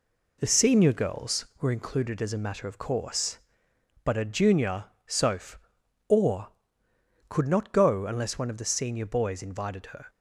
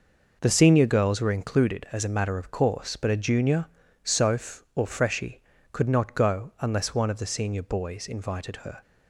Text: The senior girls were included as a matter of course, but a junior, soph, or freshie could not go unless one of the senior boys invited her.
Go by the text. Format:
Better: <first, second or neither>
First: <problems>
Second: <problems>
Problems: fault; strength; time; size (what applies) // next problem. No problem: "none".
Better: second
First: skips "freshie"; at 6.8 s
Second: none